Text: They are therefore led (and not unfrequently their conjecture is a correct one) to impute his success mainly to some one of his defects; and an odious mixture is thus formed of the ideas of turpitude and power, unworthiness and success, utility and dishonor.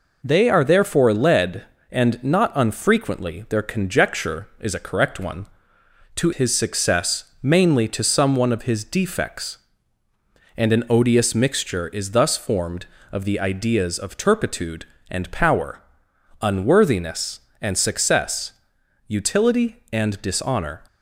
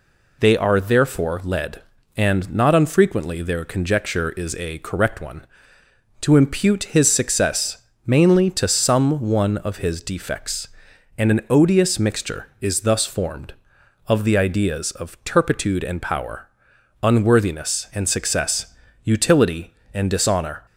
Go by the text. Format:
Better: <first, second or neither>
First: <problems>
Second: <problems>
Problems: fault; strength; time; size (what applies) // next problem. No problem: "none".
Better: second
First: skips "impute"; at 6.3 s // pauses between "success" and "mainly"; slight; at 7.2 s; 0.16 s long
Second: pauses between "success" and "mainly"; slight; at 7.7 s; 0.26 s long